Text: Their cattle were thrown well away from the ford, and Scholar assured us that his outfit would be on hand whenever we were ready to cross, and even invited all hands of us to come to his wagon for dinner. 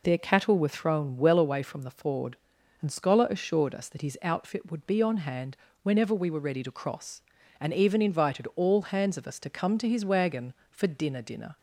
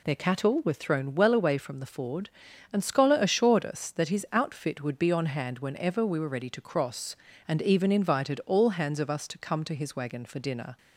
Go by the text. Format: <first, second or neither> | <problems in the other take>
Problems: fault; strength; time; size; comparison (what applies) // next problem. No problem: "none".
second | pauses between "hand" and "whenever"; slight; at 5.5 s; 0.24 s long // says "dinner" twice; at 11.2 s